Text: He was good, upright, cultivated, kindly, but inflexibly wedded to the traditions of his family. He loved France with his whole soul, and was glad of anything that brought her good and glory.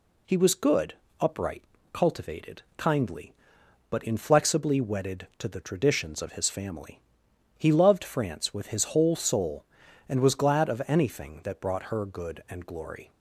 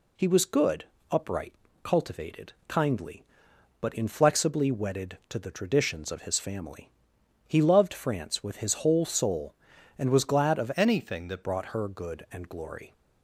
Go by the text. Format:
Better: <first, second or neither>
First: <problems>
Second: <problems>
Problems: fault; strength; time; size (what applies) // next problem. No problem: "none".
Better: first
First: none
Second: changes voice from "anything" to "that"; from 10.7 to 11.4 s; 0.7 s long